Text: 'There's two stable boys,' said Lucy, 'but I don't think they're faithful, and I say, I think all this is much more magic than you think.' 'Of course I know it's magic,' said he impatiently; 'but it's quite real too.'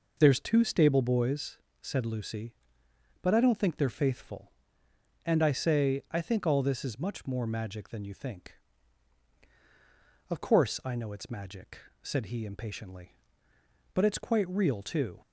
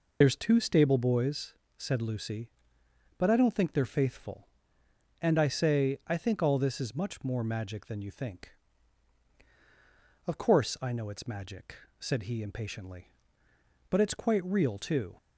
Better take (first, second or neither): first